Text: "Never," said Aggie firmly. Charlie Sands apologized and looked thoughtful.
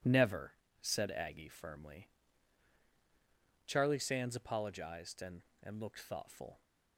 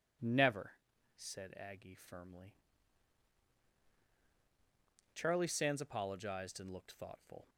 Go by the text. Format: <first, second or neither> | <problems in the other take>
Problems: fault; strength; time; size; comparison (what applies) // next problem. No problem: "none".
second | says "and" twice; at 5.6 s